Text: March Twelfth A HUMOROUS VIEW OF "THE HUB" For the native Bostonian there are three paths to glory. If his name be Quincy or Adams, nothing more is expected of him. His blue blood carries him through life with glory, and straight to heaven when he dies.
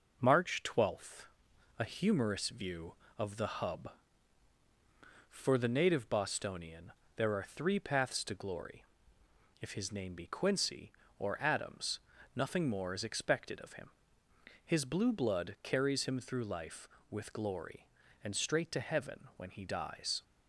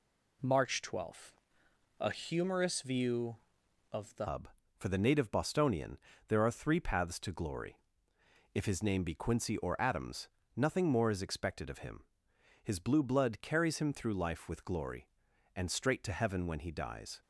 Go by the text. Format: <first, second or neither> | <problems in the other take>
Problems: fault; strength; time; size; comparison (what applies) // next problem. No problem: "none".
first | pauses between "Twelfth" and "A"; noticeable; at 1.3 s; 0.68 s long; noticeable in the first // changes voice at "HUB"; from 4.2 s on; 13.0 s long // pauses between "Bostonian" and "there"; slight; at 5.9 s; 0.30 s long; slight in the first